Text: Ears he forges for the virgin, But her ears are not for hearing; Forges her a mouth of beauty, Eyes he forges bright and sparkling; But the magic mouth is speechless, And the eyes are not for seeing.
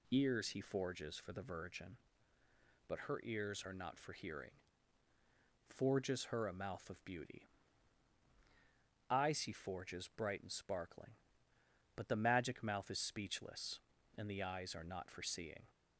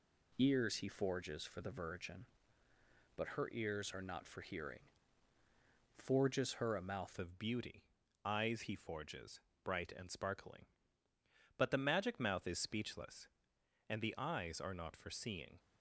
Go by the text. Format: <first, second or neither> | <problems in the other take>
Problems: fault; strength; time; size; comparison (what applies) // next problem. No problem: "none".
first | changes voice at "of"; from 7.1 s on; 8.4 s long // pauses between "forges" and "bright"; slight; at 9.4 s; 0.24 s long